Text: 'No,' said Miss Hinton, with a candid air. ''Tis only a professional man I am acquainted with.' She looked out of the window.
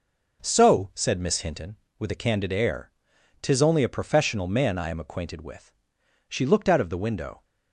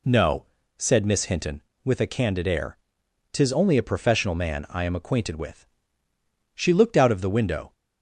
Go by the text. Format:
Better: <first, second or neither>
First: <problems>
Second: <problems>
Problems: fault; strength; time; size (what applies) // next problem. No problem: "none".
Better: second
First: says "So" for "No"; at 0.4 s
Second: none